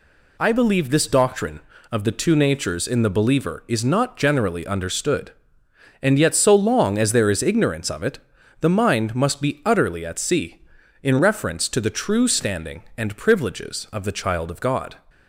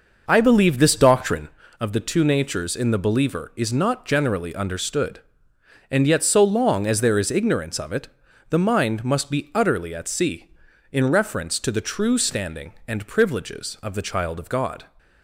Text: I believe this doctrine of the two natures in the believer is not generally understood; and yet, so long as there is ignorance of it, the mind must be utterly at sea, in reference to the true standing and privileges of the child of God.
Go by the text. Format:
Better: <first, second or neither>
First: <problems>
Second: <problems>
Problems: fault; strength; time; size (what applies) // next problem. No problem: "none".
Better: first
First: none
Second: starts louder than the rest; noticeable; until 1.5 s; 5.5 dB